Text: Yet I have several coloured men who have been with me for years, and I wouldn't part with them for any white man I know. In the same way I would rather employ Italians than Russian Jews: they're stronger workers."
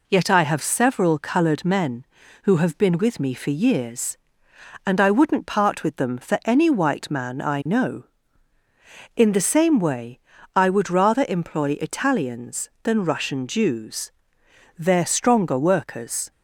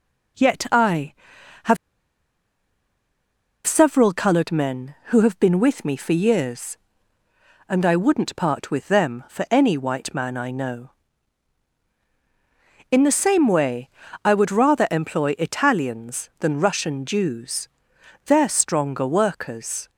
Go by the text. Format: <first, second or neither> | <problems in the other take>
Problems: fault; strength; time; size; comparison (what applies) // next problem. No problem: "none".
first | pauses between "have" and "several"; strong; at 1.7 s; 1.9 s long // pauses between "way" and "I"; slight; at 13.8 s; 0.34 s long; also in the first